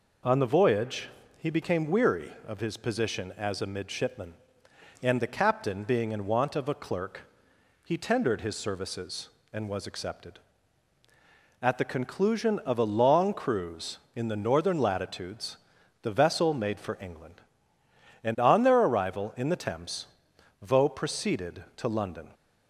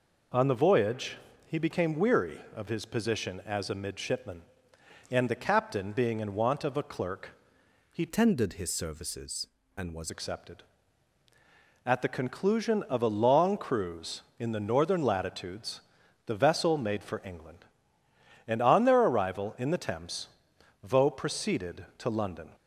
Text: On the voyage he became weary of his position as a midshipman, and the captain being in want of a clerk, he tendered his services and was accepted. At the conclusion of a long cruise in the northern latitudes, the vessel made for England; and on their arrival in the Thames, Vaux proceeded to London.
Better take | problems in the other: first | pauses between "voyage" and "he"; slight; at 1.1 s; 0.28 s long; slight in the first // changes voice from "tendered" to "was"; from 8.0 to 10.0 s; 2.0 s long

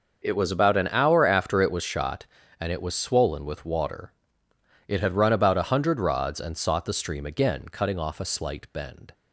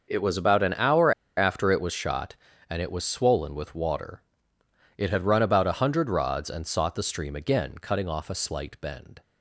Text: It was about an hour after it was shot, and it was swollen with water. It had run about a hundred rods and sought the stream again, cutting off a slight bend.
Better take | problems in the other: first | starts louder than the rest; noticeable; until 1.1 s; 6 dB; noticeable in the first // pauses between "hour" and "after"; slight; at 1.1 s; 0.26 s long

